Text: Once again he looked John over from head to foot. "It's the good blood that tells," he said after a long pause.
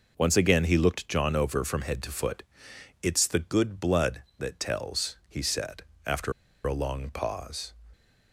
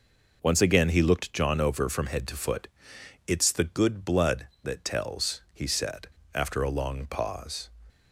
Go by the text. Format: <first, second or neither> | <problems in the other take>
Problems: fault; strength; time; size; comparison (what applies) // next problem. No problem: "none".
second | pauses between "said" and "after"; slight; at 5.8 s; 0.22 s long; slight in the second // pauses between "after" and "a"; slight; at 6.3 s; 0.34 s long